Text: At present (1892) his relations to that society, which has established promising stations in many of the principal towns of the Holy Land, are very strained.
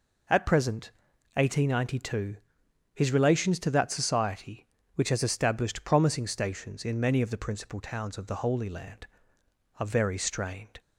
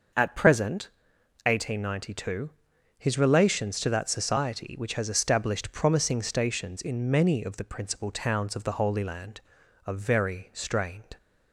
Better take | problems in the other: neither | none

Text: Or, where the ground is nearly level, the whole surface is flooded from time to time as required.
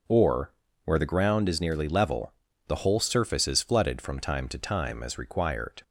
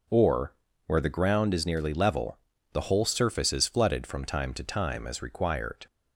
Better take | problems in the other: neither | none

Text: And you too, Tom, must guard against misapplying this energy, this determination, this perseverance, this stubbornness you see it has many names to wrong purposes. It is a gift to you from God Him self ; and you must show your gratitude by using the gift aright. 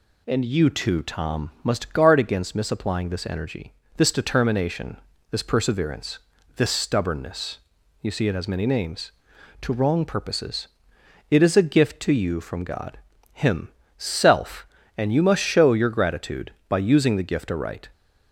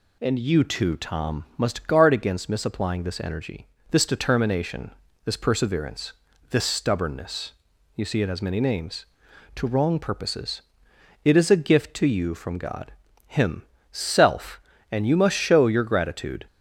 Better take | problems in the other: first | pauses between "stubbornness" and "you"; at 7.5 s; 0.44 s long; also in the first // pauses between "God" and "Him"; slight; at 12.9 s; 0.34 s long; slight in the first // pauses between "Him" and "self"; slight; at 13.6 s; 0.28 s long; slight in the first // stops before "by using the gift aright"; at 16.4 s

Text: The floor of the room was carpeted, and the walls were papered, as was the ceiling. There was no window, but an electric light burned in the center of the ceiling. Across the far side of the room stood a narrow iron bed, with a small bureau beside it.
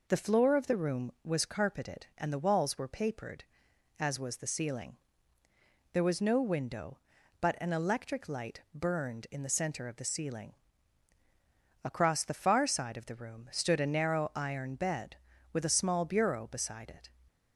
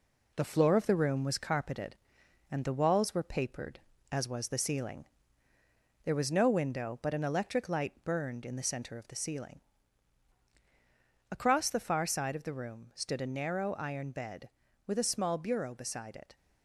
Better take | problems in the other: first | gets quieter; noticeable; throughout; 4 dB

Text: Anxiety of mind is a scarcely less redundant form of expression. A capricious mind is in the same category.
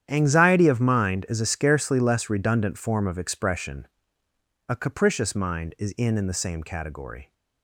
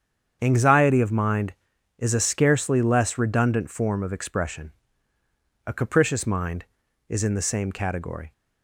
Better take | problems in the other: second | starts louder than the rest; strong; until 1.0 s; 9.5 dB; strong in the second // says "in" twice; at 6.1 s

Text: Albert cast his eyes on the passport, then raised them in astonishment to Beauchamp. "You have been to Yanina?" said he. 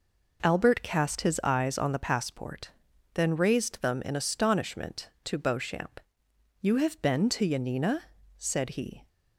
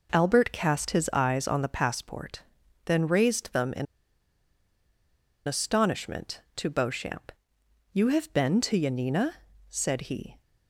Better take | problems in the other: first | pauses between "in" and "astonishment"; strong; at 3.8 s; 1.6 s long

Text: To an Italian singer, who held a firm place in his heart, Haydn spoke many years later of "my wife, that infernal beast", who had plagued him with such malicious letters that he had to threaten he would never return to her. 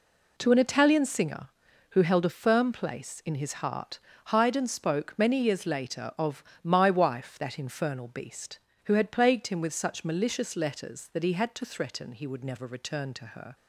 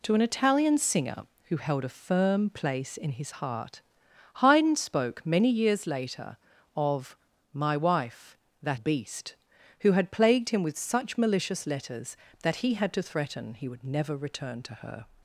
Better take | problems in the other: first | pauses between "of" and "my"; at 7.1 s; 0.38 s long; slight in the first // skips "infernal"; at 8.7 s

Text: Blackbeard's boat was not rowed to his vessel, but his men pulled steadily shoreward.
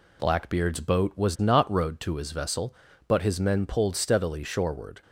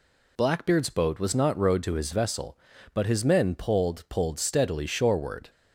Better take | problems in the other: first | says "pulled" twice; at 4.0 s

